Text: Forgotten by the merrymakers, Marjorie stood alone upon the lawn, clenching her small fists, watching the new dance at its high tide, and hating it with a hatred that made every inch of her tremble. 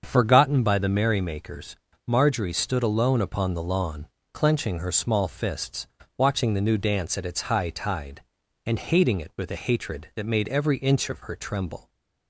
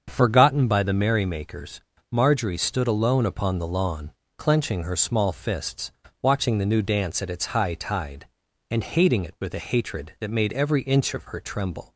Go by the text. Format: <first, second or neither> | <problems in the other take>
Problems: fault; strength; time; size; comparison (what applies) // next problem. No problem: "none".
neither | starts louder than the rest; the same in both